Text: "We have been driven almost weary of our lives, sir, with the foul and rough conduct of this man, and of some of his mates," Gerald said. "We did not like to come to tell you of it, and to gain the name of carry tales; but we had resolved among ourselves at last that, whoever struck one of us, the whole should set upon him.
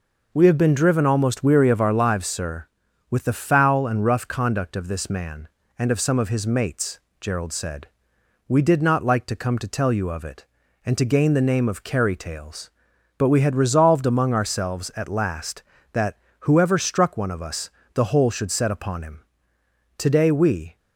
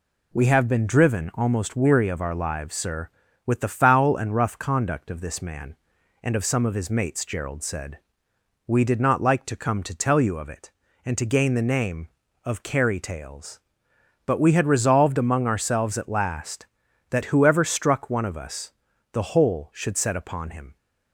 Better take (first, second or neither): second